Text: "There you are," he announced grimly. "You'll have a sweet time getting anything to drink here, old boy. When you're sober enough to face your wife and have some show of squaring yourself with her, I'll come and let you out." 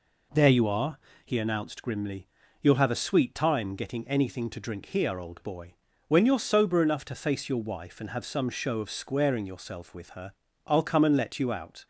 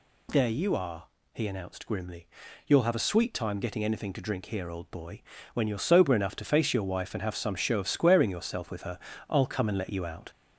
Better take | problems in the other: first | gets louder; slight; throughout; 3 dB

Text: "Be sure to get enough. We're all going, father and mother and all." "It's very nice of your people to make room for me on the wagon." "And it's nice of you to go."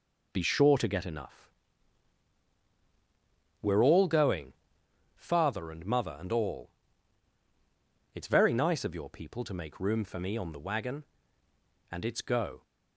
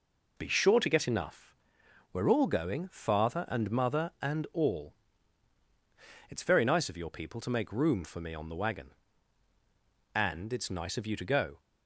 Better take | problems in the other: second | skips "nice of you to"; at 12.2 s

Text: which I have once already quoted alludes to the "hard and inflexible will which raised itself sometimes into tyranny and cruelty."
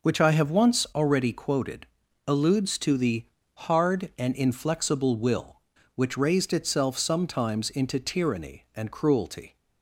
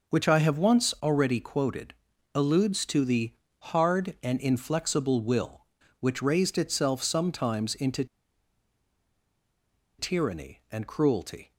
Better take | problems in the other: first | pauses between "quoted" and "alludes"; at 1.9 s; 0.42 s long; also in the first // pauses between "the" and "hard"; at 3.3 s; 0.40 s long; also in the first // pauses between "into" and "tyranny"; strong; at 8.0 s; 1.9 s long

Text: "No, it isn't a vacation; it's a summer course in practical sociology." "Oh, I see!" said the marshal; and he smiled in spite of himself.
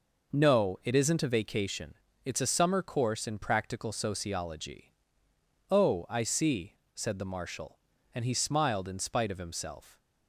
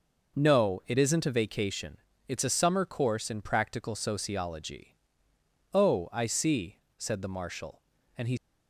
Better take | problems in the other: first | stops before "smiled in spite of himself"; at 8.3 s

